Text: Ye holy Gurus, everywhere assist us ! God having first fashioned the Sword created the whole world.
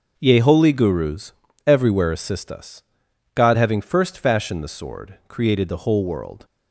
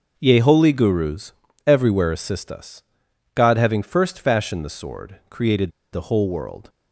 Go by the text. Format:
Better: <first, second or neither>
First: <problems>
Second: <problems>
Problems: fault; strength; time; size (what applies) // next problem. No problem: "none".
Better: first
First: starts louder than the rest; until 1.1 s; 6.5 dB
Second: starts louder than the rest; until 1.1 s; 6.5 dB // pauses between "created" and "the"; slight; at 5.7 s; 0.21 s long